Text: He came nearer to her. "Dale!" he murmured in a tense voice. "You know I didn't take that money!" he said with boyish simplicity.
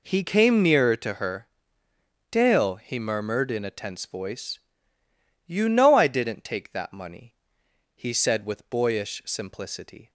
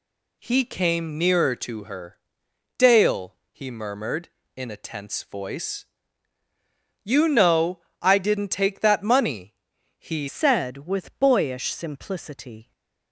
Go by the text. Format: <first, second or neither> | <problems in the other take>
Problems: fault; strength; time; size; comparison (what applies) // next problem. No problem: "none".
first | pauses between "know" and "I"; slight; at 7.8 s; 0.18 s long // changes voice at "said"; from 10.2 s on; 2.5 s long